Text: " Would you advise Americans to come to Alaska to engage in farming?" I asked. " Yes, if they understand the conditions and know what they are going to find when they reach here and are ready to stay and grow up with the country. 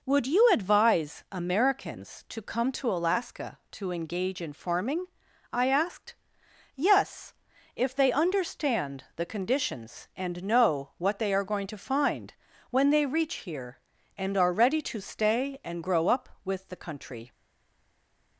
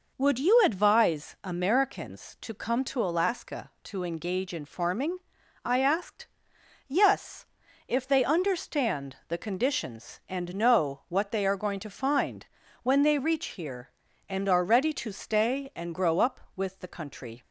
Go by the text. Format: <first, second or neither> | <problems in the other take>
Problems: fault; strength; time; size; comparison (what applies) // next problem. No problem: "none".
second | pauses between "find" and "when"; at 12.3 s; 0.38 s long; also in the second // stays silent after the last word; from 17.3 s on; 1.0 s long